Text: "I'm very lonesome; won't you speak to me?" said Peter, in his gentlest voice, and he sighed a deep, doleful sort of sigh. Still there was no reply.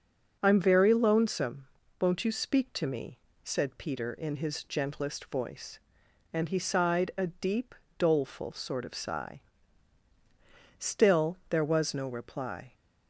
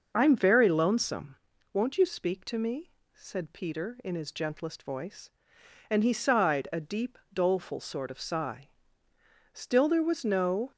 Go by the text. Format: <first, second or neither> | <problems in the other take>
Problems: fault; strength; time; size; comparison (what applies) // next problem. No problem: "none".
first | stops before "reply"; at 10.7 s